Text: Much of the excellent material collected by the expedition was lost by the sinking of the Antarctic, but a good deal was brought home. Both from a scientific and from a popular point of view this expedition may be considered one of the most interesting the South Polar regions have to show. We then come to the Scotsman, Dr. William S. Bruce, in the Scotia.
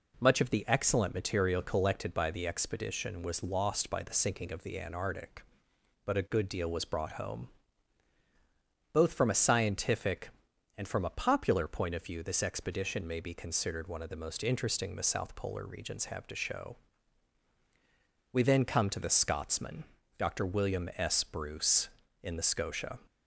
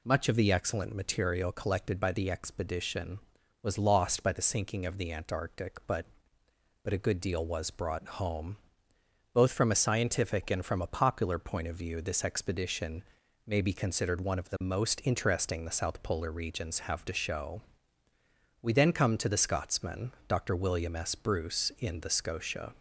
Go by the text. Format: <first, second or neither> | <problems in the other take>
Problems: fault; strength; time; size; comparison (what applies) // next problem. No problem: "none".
first | says "but" twice; at 6.8 s // pauses between "expedition" and "may"; at 13.0 s; 0.44 s long